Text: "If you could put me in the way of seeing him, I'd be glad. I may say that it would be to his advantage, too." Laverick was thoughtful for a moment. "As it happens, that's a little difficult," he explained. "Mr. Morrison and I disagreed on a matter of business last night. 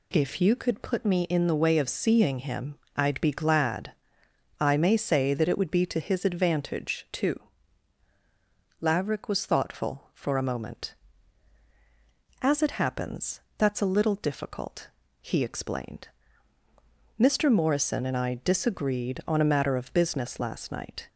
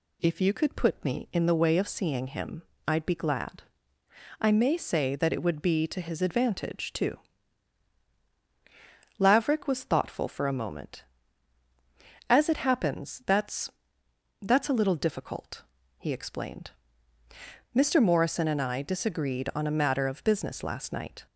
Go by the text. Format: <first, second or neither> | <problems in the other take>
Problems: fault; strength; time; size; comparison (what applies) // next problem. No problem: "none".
first | says "that's" twice; at 14.4 s